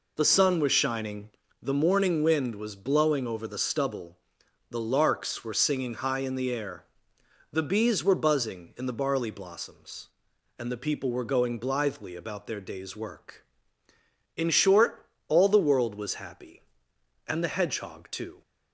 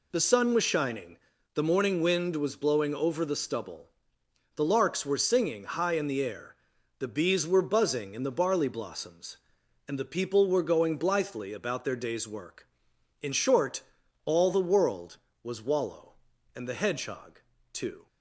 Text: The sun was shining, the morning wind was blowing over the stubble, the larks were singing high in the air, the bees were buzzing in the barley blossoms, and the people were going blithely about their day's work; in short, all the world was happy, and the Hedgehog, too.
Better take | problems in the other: first | says "wallow" for "happy"; at 15.6 s

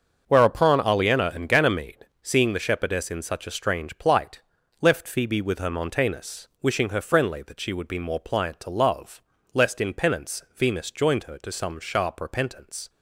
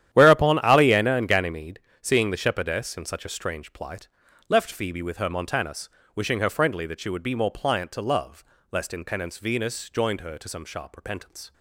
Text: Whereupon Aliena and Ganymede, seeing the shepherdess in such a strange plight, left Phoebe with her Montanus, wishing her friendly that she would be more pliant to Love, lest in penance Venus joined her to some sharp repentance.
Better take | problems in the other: first | gets quieter; strong; throughout; 14 dB // starts louder than the rest; strong; until 1.1 s; 11 dB; also in the first

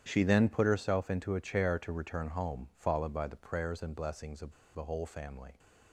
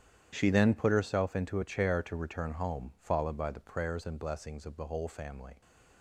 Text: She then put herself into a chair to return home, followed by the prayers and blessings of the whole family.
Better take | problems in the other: second | starts louder than the rest; strong; until 1.0 s; 9.5 dB; strong in the second // pauses between "of" and "the"; slight; at 4.5 s; 0.21 s long

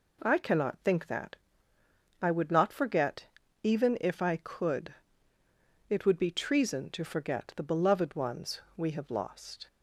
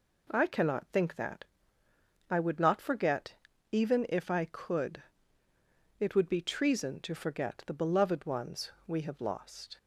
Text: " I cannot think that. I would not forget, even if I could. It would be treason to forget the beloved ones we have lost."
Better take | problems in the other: neither | pauses between "ones" and "we"; slight; the same in both

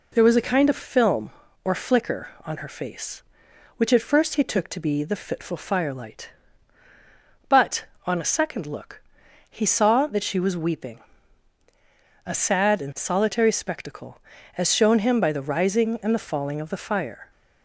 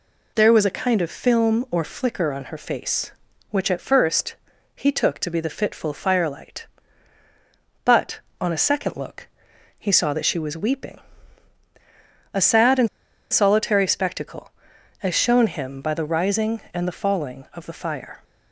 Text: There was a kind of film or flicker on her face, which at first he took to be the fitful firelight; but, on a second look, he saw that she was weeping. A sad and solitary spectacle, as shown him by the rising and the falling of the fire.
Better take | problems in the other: first | pauses between "first" and "he"; at 4.3 s; 0.42 s long // pauses between "and" and "solitary"; at 12.8 s; 0.42 s long

